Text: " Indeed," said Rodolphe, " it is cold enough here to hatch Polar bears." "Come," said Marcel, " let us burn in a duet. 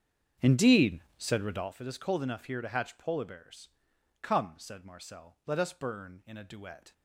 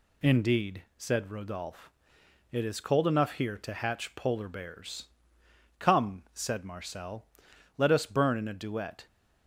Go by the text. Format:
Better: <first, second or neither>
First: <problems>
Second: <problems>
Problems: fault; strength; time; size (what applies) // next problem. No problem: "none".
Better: second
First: starts louder than the rest; strong; until 1.8 s; 7.5 dB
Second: none